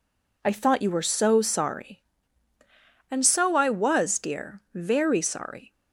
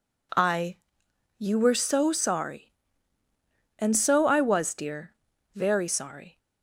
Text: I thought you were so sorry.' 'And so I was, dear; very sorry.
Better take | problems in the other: first | skips "thought"; at 1.0 s

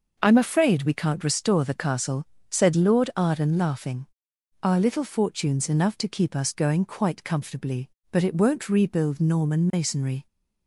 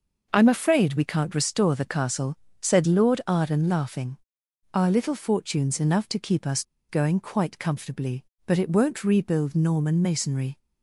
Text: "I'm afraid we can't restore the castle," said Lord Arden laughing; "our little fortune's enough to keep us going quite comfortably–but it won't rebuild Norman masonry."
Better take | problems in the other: first | pauses between "us" and "going"; slight; at 6.6 s; 0.24 s long

